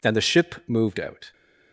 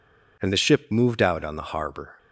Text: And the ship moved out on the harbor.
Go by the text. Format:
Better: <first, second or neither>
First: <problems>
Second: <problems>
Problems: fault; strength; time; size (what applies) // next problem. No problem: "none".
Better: second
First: stops before "on the harbor"; at 1.3 s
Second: none